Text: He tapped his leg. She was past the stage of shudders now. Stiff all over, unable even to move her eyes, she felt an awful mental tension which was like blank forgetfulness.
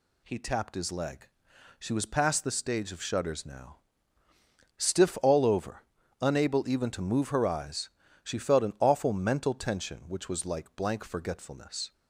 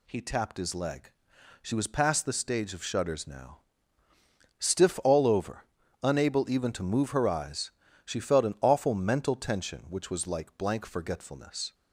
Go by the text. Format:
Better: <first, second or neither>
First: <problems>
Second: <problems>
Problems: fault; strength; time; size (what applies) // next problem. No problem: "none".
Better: neither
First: none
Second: none